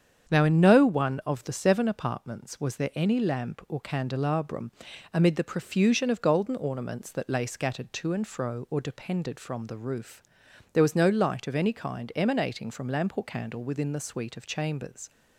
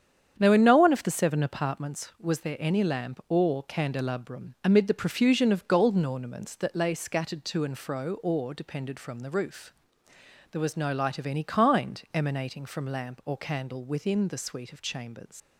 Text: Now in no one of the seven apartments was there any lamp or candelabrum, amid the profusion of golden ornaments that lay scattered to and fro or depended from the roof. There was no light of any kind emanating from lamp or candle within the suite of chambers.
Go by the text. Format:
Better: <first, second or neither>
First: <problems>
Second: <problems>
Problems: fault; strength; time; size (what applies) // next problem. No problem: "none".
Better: first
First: starts louder than the rest; strong; until 1.3 s; 8 dB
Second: starts louder than the rest; strong; until 1.3 s; 8.5 dB // leaves "chambers" unfinished; at 15.4 s; 145 ms